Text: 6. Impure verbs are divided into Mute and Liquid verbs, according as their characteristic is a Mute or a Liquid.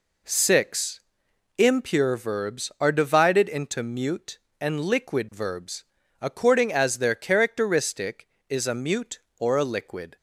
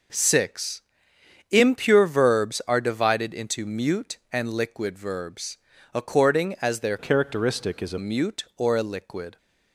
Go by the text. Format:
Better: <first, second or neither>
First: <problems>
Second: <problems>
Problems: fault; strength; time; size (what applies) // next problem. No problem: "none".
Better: first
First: none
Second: changes voice from "characteristic" to "a"; from 6.9 to 7.9 s; 1.0 s long